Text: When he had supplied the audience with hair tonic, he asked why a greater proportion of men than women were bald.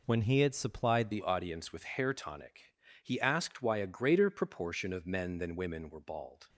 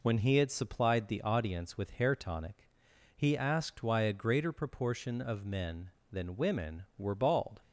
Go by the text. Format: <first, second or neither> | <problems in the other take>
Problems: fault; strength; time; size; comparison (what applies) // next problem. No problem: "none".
second | changes voice at "the"; from 1.1 s on; 5.3 s long